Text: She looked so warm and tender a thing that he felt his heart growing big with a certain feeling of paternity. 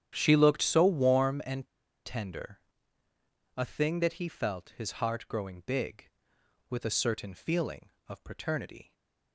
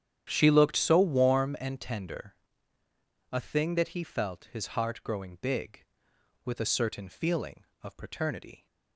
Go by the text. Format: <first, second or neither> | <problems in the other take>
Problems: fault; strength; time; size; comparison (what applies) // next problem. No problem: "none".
second | starts louder than the rest; strong; until 1.1 s; 10 dB; strong in the second // pauses between "and" and "tender"; at 1.6 s; 0.39 s long // pauses between "tender" and "a"; noticeable; at 2.5 s; 0.98 s long; noticeable in the second // stays silent after the last word; slight; from 8.8 s on; 0.5 s long